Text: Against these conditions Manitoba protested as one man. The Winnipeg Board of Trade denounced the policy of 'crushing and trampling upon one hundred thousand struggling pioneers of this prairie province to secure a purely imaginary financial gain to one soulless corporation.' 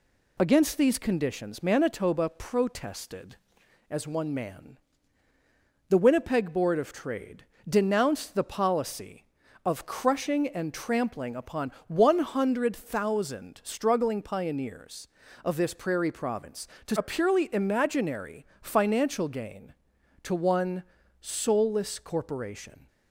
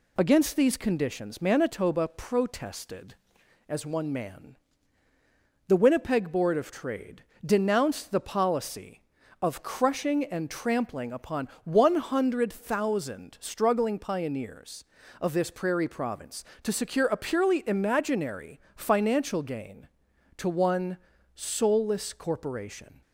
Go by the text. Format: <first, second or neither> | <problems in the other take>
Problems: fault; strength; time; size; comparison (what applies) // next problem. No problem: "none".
second | pauses between "Trade" and "denounced"; slight; at 7.4 s; 0.24 s long; slight in the second // pauses between "upon" and "one"; slight; at 11.7 s; 0.16 s long; slight in the second // skips "secure"; at 16.9 s // pauses between "imaginary" and "financial"; slight; at 18.4 s; 0.16 s long; slight in the second // pauses between "one" and "soulless"; at 20.8 s; 0.38 s long; also in the second